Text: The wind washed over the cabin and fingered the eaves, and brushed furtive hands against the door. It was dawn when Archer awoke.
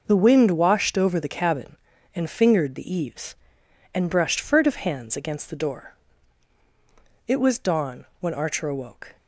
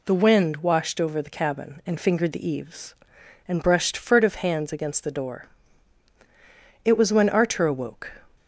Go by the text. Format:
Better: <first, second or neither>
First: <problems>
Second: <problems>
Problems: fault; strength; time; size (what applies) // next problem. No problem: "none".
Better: first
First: none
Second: skips "dawn"; at 7.1 s